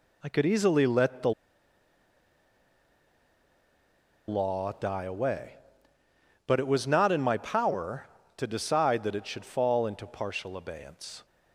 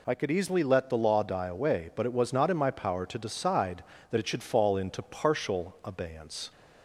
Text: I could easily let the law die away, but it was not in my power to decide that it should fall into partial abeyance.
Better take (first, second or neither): second